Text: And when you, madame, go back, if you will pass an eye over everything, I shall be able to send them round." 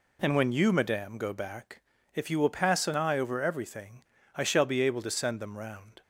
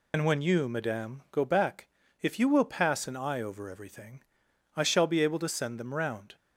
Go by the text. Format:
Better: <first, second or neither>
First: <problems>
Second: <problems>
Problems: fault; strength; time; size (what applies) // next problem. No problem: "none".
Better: first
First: none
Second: loses the start of "And"; at 0.1 s; 80 ms